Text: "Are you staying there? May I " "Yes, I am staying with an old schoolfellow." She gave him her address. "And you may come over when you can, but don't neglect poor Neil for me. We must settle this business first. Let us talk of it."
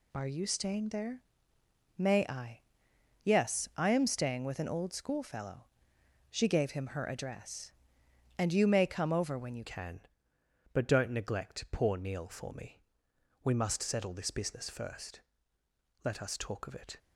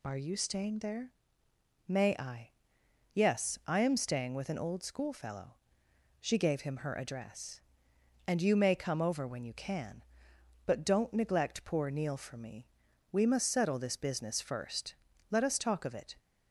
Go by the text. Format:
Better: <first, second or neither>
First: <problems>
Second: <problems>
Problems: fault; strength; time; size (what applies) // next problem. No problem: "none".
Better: second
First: changes voice at "can"; from 9.6 s on; 7.3 s long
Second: none